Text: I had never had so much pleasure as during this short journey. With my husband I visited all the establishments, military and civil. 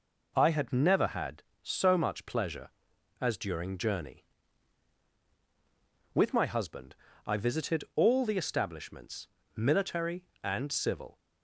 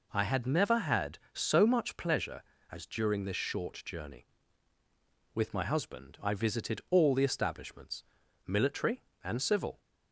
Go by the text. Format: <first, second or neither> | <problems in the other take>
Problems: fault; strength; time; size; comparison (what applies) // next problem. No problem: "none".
second | skips "this short"; at 3.7 s // pauses between "husband" and "I"; slight; at 6.9 s; 0.32 s long